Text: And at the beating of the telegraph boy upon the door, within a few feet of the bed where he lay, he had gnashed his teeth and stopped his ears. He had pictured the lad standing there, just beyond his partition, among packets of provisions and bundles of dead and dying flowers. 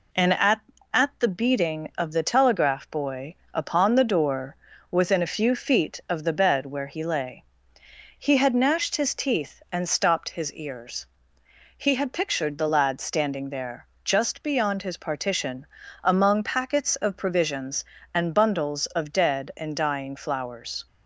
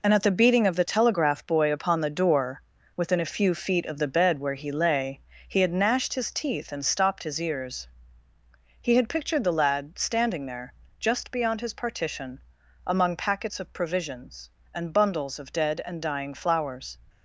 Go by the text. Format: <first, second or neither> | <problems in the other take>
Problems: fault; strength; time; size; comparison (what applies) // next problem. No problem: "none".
second | says "at" twice; at 0.9 s // pauses between "boy" and "upon"; slight; at 3.3 s; 0.18 s long